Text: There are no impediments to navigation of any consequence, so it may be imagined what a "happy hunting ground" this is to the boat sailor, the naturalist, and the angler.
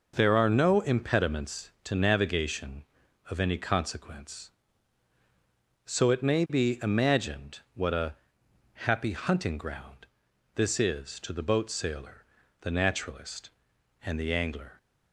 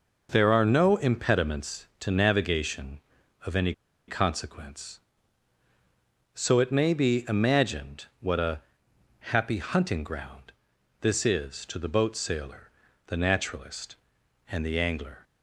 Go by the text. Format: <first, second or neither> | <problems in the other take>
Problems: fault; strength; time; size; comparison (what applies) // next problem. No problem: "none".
first | pauses between "any" and "consequence"; slight; at 3.7 s; 0.35 s long // pauses between "imagined" and "what"; slight; at 8.0 s; 0.16 s long; slight in the first // pauses between "a" and "happy"; noticeable; at 8.6 s; 0.72 s long; noticeable in the first // pauses between "ground" and "this"; noticeable; at 10.5 s; 0.48 s long; noticeable in the first